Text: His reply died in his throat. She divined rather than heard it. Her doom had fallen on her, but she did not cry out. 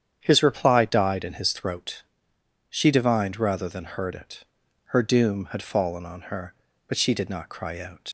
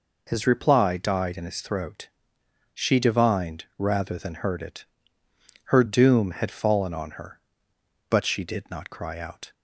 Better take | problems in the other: second | starts louder than the rest; strong; until 1.2 s; 9 dB // leaves "out" unfinished; at 8.0 s; 85 ms

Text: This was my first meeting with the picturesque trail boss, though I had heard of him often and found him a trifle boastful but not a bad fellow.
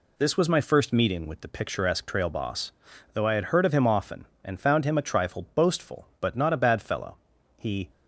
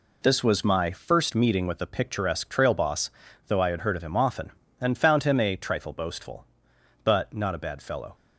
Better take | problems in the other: second | goes on to say "He"; slight; from 7.5 s on; 0.32 s long

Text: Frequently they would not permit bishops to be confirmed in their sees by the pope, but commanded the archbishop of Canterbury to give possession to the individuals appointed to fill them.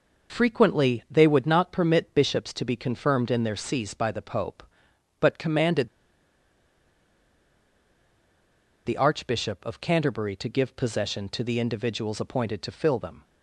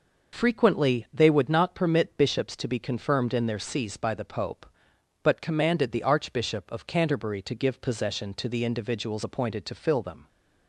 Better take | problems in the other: second | pauses between "commanded" and "the"; strong; at 5.8 s; 2.9 s long

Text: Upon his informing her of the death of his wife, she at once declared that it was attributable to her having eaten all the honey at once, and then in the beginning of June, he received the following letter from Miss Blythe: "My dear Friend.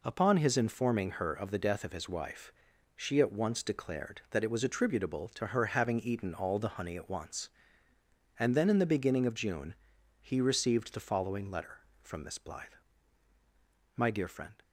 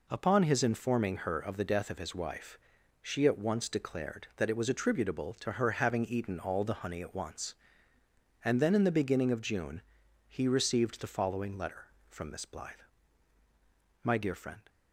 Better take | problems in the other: neither | none

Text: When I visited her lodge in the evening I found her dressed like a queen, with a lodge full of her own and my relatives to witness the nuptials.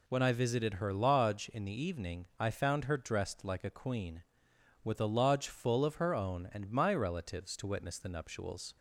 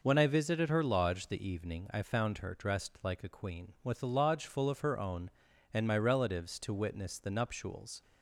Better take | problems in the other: first | skips "in"; at 1.2 s

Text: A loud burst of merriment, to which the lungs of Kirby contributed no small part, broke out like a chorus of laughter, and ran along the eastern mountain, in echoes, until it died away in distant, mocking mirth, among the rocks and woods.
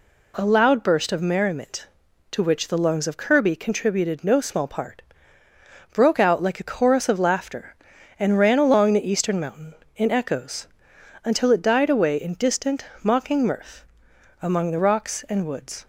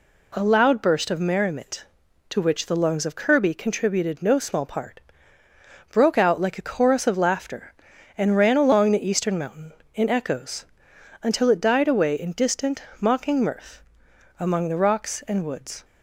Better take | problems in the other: neither | none

